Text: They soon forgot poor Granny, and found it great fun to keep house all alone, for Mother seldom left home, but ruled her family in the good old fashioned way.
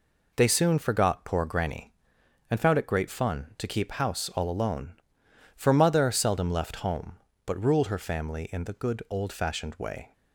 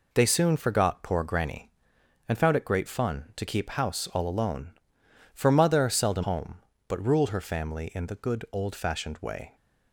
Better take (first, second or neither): first